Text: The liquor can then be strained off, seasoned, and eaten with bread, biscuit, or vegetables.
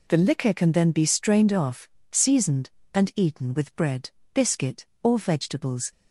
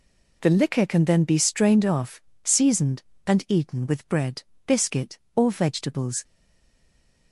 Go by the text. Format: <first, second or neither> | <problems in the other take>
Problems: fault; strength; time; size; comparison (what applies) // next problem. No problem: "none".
first | stays silent after the last word; from 6.2 s on; 1.1 s long